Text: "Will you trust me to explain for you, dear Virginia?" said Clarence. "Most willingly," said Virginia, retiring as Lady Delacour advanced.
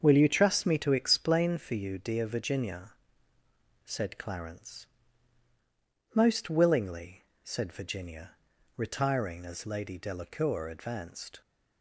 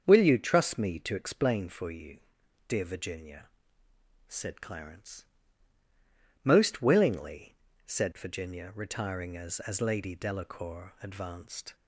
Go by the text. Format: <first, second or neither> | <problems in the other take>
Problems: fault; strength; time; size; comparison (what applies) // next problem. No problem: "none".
first | starts louder than the rest; until 1.0 s; 7 dB; also in the first // says "as" twice; at 9.6 s